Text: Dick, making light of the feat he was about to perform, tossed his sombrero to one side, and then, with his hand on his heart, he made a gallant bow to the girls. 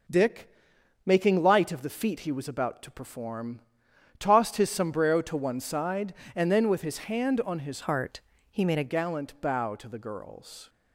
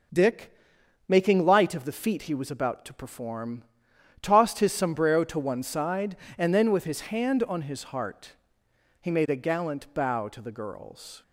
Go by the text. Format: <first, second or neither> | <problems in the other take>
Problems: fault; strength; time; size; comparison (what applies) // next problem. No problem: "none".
second | changes voice from "heart" to "a"; from 7.8 to 8.8 s; 1.0 s long